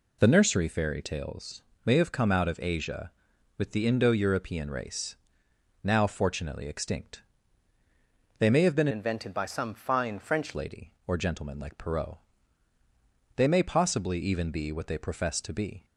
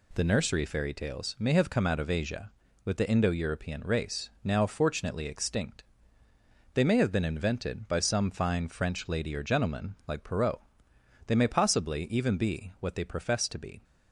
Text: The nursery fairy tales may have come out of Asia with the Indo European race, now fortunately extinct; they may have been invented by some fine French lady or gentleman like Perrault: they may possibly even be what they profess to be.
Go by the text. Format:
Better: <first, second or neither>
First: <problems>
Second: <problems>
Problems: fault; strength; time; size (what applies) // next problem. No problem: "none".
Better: second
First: pauses between "tales" and "may"; slight; at 1.6 s; 0.22 s long // changes voice from "invented" to "French"; from 8.9 to 10.5 s; 1.6 s long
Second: none